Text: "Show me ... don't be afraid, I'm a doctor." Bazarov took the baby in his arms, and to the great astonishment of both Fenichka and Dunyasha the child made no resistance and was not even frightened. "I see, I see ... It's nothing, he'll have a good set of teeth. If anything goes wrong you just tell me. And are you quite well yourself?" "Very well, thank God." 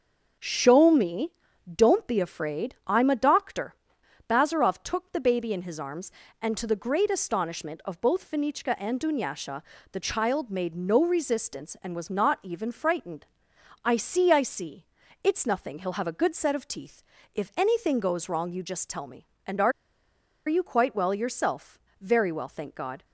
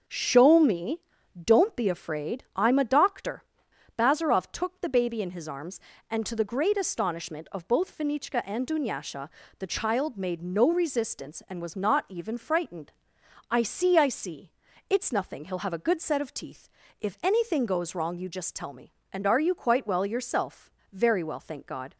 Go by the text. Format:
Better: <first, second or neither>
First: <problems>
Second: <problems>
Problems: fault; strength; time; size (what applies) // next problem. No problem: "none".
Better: second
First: starts louder than the rest; until 1.8 s; 7 dB // pauses between "Dunyasha" and "the"; slight; at 9.6 s; 0.30 s long // pauses between "are" and "you"; noticeable; at 19.7 s; 0.76 s long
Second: starts louder than the rest; until 1.4 s; 7 dB // pauses between "Dunyasha" and "the"; slight; at 9.2 s; 0.30 s long